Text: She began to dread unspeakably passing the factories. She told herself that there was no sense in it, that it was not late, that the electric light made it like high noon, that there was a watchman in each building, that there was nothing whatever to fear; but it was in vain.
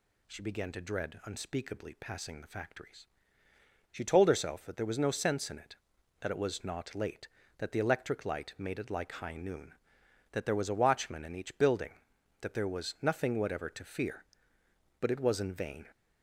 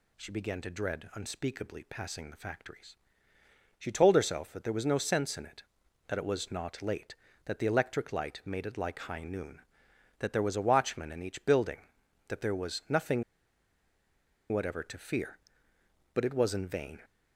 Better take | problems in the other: first | pauses between "nothing" and "whatever"; strong; at 13.2 s; 1.2 s long

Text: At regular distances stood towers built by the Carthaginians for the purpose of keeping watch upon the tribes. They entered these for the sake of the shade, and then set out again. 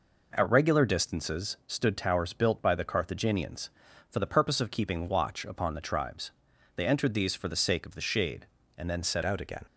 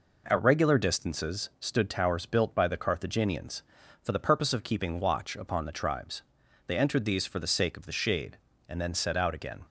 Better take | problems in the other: second | changes voice at "out"; from 9.2 s on; 0.4 s long

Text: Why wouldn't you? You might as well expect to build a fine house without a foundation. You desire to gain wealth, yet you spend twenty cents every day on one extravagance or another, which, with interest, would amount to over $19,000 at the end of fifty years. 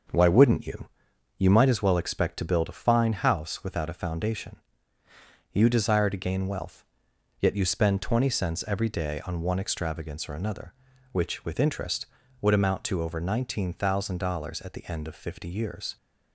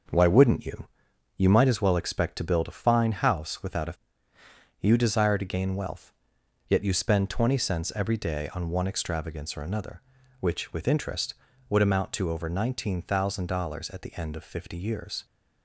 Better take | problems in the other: first | starts louder than the rest; until 1.6 s; 6.5 dB; also in the first // skips "foundation"; at 4.3 s

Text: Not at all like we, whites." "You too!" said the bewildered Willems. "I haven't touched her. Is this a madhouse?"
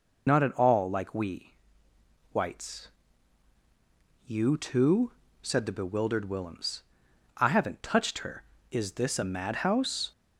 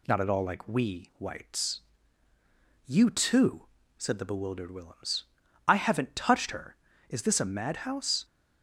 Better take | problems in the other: second | loses the start of "Not"; at 0.2 s; 45 ms

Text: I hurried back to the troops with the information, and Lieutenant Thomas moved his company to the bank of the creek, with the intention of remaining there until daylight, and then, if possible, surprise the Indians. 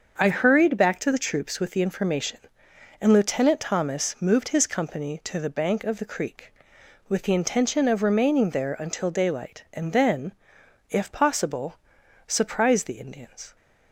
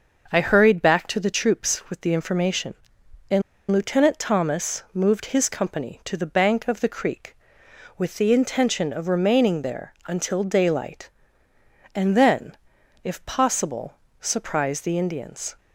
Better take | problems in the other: first | starts louder than the rest; until 1.3 s; 6 dB; also in the first // pauses between "and" and "Lieutenant"; slight; at 3.4 s; 0.29 s long

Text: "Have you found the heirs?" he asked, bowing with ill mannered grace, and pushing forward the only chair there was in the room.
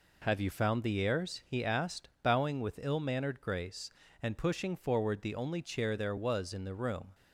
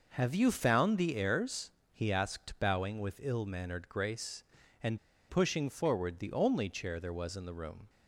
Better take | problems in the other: first | pauses between "and" and "pushing"; slight; at 4.9 s; 0.30 s long

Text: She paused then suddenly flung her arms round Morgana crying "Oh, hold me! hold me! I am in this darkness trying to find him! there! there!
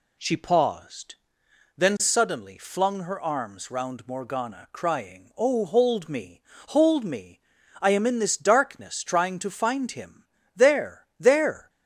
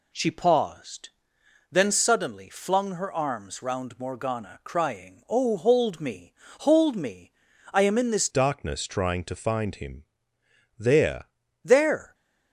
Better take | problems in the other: first | pauses between "paused" and "then"; noticeable; at 1.0 s; 0.62 s long; noticeable in the first // changes voice from "darkness" to "there"; from 8.2 to 11.2 s; 3.0 s long

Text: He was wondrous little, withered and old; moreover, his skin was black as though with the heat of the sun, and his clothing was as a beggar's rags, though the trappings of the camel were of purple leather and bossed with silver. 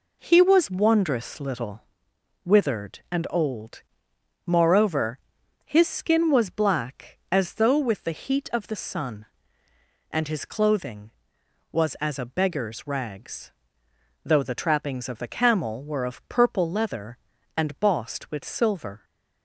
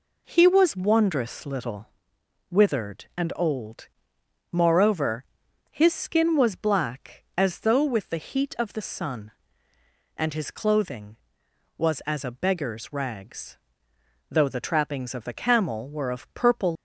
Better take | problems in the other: first | stops before "leather and bossed with silver"; at 16.7 s

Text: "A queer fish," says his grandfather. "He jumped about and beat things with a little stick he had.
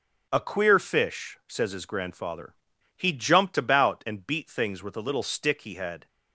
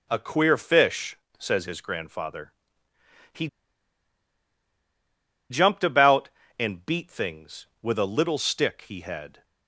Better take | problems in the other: first | starts louder than the rest; until 1.1 s; 7 dB; strong in the first // pauses between "He" and "jumped"; strong; at 3.4 s; 2.0 s long

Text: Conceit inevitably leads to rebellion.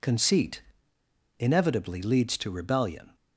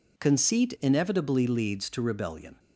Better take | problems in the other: second | pauses between "Conceit" and "inevitably"; noticeable; at 0.6 s; 0.75 s long

